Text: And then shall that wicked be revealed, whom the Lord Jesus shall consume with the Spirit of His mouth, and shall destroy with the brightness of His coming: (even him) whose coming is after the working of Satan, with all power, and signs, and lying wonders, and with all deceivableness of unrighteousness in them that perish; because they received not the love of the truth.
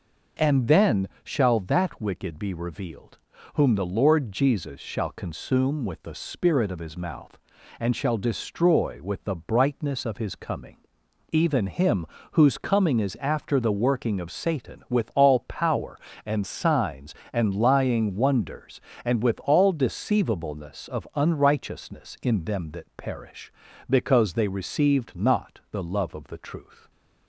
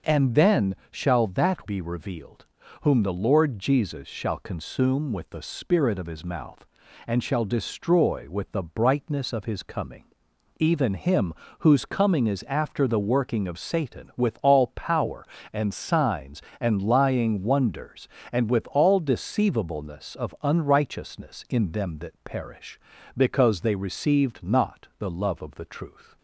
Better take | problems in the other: first | pauses between "then" and "shall"; slight; at 0.7 s; 0.16 s long; slight in the first // skips "wicked"; at 1.6 s

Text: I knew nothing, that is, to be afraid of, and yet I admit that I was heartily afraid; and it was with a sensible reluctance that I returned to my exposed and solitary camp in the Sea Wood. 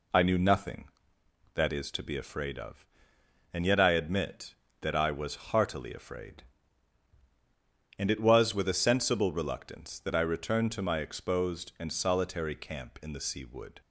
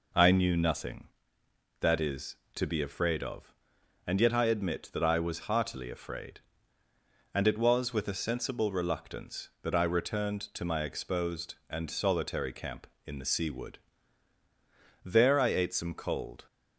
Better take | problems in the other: first | goes on to say "There I ate some cold"; from 15.0 s on; 1.4 s long

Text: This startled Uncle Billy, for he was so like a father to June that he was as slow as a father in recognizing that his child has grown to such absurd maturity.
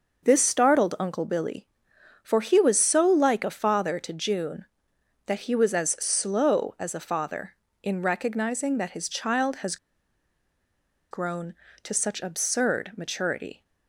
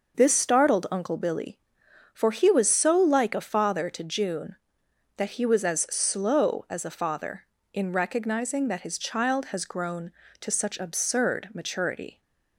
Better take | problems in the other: second | pauses between "has" and "grown"; strong; at 9.7 s; 1.3 s long

